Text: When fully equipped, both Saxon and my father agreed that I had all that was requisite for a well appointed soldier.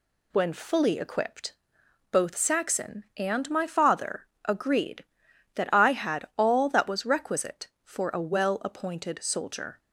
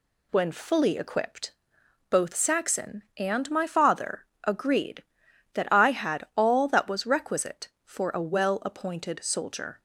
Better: neither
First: pauses between "father" and "agreed"; slight; at 4.2 s; 0.18 s long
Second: pauses between "father" and "agreed"; slight; at 4.2 s; 0.18 s long

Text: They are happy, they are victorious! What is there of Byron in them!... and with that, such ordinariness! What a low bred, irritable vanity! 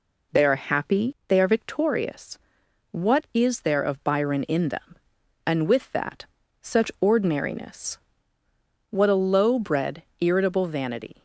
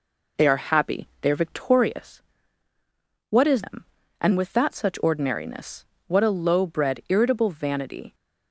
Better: first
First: none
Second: skips "there of Byron in"; at 3.6 s

